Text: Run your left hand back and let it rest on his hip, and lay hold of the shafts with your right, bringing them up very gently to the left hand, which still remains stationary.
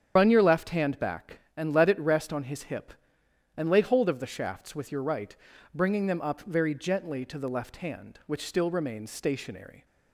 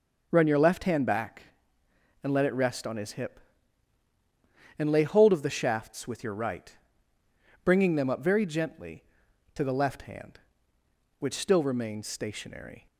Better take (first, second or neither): second